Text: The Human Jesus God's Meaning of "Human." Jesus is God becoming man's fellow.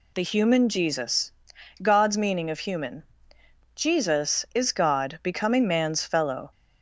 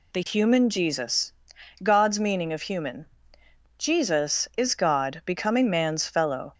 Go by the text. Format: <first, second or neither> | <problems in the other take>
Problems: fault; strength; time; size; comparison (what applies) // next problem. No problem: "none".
neither | pauses between "Jesus" and "God's"; noticeable; the same in both